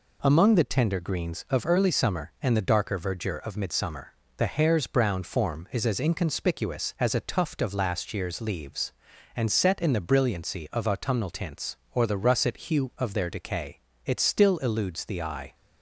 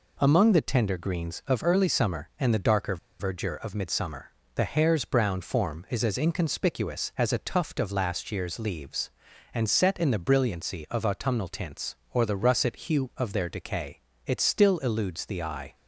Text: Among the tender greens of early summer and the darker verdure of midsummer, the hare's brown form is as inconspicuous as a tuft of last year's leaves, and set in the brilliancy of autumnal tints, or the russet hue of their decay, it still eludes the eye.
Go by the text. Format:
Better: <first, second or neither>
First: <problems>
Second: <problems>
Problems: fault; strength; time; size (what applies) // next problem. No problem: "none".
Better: first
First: none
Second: pauses between "darker" and "verdure"; slight; at 2.9 s; 0.23 s long